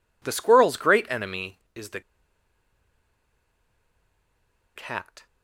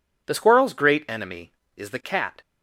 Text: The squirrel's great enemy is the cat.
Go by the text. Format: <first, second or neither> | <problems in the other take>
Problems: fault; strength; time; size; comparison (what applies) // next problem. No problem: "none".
second | pauses between "the" and "cat"; strong; at 2.0 s; 2.7 s long